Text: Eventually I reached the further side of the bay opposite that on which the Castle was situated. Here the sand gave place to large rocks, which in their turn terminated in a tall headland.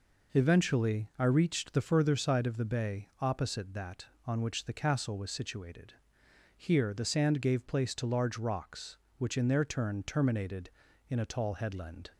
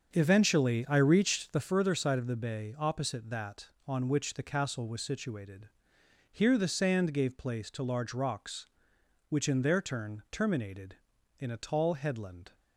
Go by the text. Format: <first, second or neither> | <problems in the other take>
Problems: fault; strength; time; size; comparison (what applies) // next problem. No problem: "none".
first | starts louder than the rest; until 1.7 s; 7 dB